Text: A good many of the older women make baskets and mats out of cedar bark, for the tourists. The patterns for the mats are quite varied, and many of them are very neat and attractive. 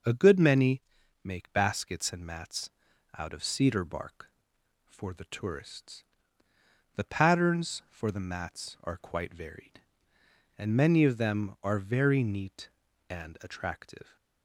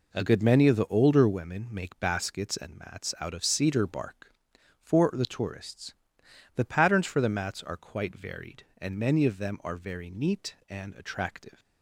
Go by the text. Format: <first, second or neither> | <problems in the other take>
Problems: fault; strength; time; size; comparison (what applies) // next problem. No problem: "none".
second | skips "of the older women"; at 1.0 s // pauses between "mats" and "out"; noticeable; at 2.7 s; 0.48 s long